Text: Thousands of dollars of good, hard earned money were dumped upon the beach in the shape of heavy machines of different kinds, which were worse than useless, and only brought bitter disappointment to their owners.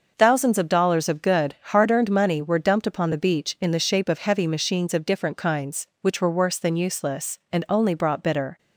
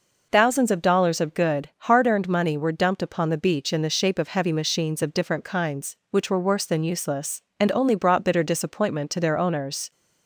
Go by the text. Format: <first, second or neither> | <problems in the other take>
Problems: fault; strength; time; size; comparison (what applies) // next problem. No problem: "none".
second | starts louder than the rest; noticeable; until 1.1 s; 6 dB // stops before "disappointment to their owners"; at 8.5 s